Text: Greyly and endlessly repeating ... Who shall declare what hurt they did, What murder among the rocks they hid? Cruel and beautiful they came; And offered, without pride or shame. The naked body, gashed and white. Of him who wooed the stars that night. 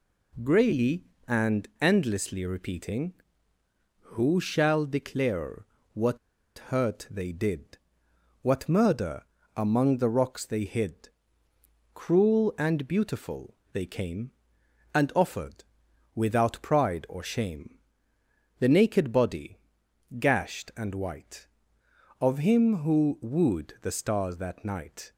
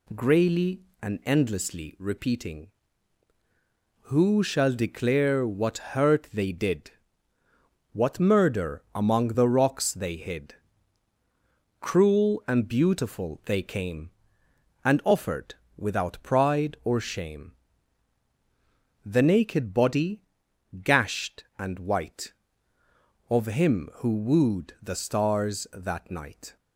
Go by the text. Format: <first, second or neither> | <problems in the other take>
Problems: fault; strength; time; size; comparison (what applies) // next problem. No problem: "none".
second | pauses between "declare" and "what"; slight; at 5.6 s; 0.28 s long // pauses between "what" and "hurt"; noticeable; at 6.1 s; 0.49 s long // pauses between "murder" and "among"; slight; at 9.2 s; 0.32 s long // pauses between "beautiful" and "they"; slight; at 13.5 s; 0.18 s long